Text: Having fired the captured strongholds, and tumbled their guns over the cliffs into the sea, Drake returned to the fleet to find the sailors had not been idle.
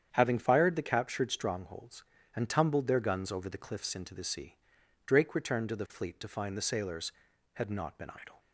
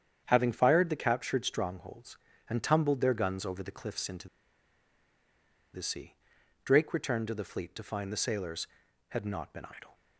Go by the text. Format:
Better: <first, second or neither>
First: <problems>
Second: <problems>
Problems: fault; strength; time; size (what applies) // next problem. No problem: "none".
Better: first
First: starts louder than the rest; strong; until 1.1 s; 8.5 dB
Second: starts louder than the rest; strong; until 1.2 s; 8.5 dB // pauses between "into" and "the"; strong; at 4.2 s; 1.4 s long